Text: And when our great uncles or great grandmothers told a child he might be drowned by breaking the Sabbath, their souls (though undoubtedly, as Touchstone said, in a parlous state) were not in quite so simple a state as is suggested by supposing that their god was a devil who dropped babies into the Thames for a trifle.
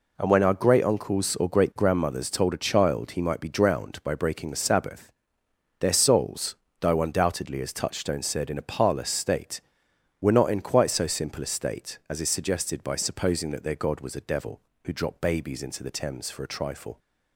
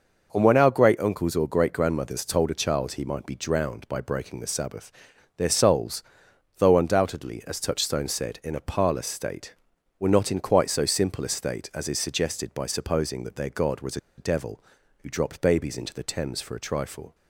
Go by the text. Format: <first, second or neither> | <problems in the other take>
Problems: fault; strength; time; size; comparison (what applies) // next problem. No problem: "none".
first | pauses between "was" and "a"; slight; at 13.9 s; 0.20 s long